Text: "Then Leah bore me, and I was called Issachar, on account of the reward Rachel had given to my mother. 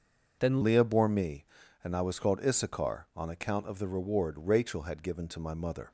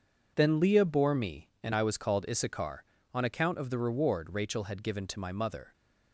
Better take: second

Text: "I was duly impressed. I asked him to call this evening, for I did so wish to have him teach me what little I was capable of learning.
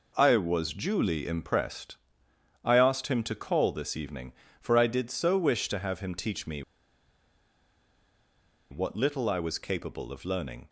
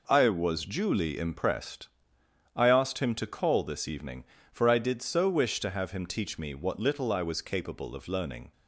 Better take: second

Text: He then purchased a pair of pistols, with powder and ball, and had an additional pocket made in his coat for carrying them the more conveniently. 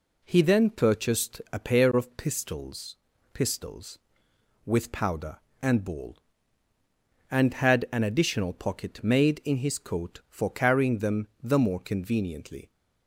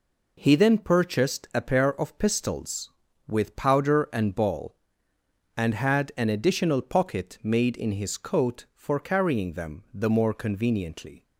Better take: second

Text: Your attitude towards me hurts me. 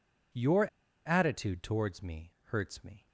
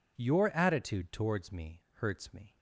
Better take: second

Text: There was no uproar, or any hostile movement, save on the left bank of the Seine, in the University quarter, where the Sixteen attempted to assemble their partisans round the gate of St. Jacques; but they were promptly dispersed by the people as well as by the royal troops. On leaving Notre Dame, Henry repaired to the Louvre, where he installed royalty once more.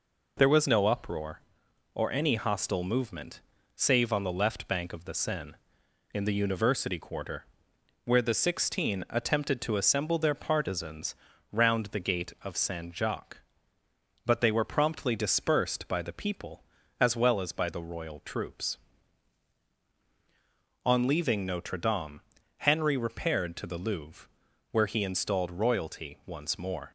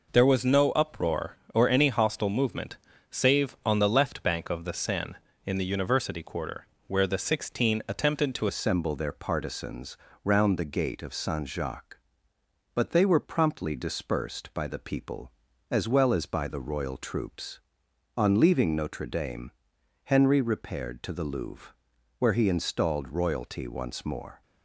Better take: first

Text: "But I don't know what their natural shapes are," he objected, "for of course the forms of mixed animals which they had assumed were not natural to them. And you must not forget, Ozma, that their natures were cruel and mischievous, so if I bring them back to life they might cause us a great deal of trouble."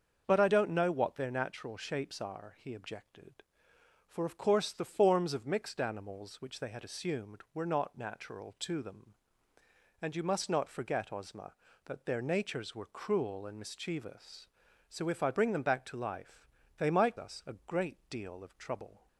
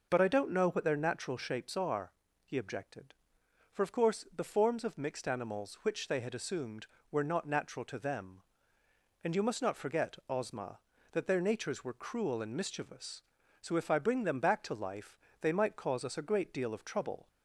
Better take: second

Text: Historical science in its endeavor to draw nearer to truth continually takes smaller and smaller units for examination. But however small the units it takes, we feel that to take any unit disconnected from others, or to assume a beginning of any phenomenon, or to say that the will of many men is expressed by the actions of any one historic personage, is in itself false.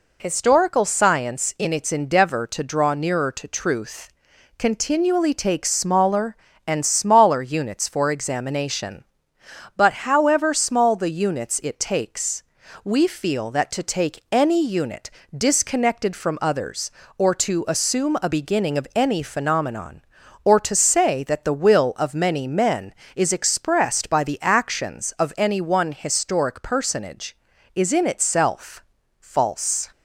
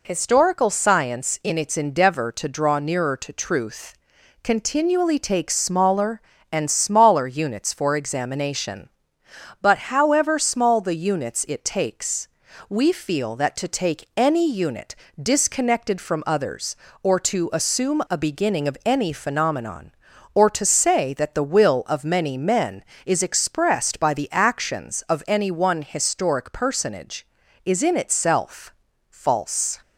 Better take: neither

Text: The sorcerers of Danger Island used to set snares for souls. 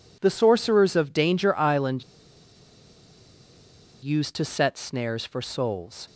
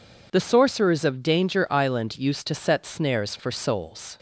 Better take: second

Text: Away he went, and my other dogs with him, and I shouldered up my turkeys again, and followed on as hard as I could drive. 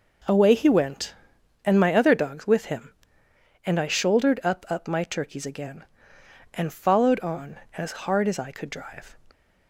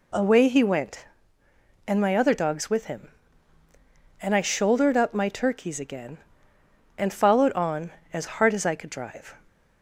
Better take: second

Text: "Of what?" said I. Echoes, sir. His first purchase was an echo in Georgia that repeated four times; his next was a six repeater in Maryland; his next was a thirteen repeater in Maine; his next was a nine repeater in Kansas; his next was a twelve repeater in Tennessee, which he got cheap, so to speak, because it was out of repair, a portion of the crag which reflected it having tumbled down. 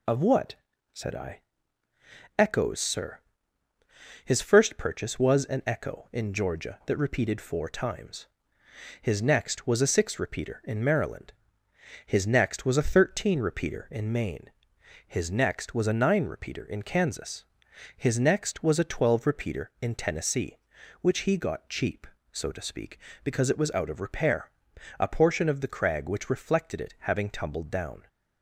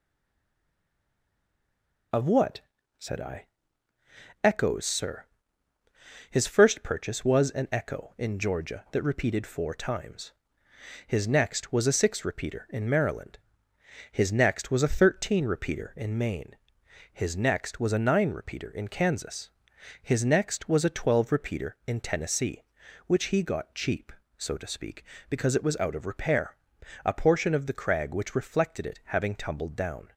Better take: first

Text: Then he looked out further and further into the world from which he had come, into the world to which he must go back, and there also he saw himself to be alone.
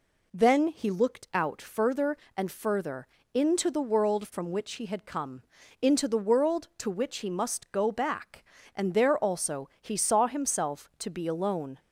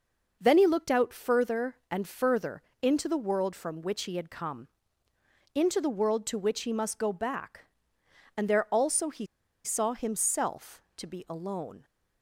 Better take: first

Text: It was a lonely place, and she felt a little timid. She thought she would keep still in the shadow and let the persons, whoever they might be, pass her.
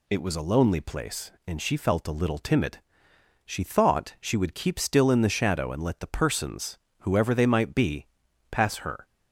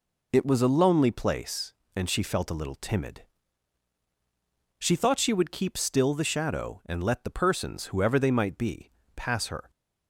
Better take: first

